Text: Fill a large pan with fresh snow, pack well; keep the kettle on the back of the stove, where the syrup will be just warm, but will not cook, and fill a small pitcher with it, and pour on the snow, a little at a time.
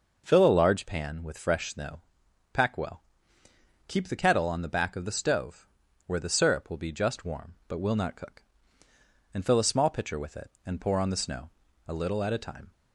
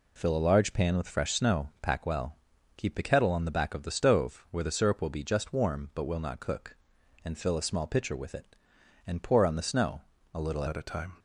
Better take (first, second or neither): first